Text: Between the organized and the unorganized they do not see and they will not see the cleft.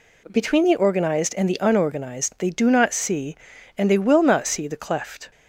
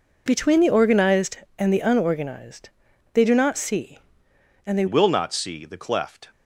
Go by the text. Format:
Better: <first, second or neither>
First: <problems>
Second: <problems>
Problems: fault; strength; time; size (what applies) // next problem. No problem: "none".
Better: first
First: none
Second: pauses between "unorganized" and "they"; noticeable; at 2.6 s; 0.46 s long // changes voice at "will"; from 4.8 s on; 1.4 s long